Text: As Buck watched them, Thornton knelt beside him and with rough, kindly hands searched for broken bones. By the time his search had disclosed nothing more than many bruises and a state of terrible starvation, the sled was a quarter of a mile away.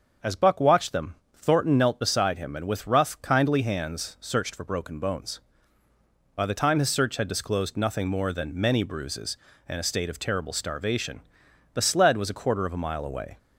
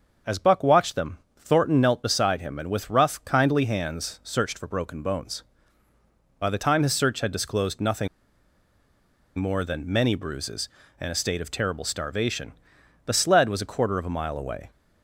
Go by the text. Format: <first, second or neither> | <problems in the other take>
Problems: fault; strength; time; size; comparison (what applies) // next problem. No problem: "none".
first | starts louder than the rest; until 1.4 s; 6.5 dB; also in the first // pauses between "nothing" and "more"; strong; at 8.0 s; 1.3 s long